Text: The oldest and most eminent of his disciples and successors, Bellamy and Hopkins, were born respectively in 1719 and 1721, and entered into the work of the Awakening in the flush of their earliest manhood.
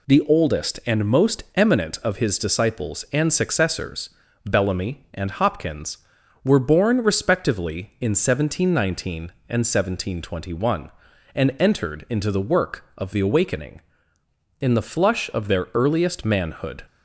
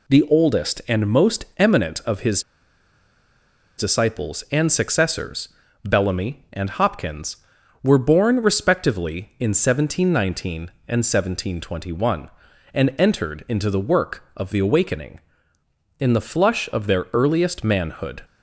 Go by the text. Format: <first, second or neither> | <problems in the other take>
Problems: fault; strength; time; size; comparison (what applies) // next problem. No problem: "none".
first | pauses between "his" and "disciples"; strong; at 2.4 s; 1.3 s long